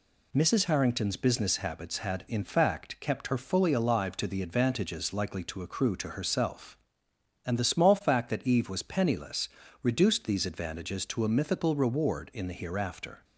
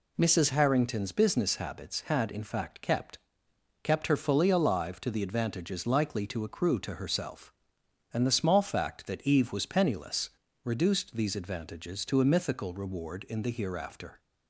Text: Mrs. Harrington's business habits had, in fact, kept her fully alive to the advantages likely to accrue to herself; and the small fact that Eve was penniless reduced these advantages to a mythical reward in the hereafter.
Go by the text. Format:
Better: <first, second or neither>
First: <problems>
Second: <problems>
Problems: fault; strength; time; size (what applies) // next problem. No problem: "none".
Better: first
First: pauses between "penniless" and "reduced"; slight; at 9.4 s; 0.32 s long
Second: says "kept" twice; at 3.8 s // pauses between "penniless" and "reduced"; slight; at 10.2 s; 0.34 s long